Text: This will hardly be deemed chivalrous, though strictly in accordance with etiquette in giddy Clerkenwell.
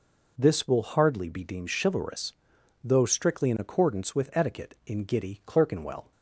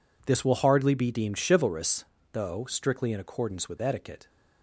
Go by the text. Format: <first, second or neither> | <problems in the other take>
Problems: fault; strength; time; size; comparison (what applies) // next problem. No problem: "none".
first | stops before "in giddy Clerkenwell"; at 4.2 s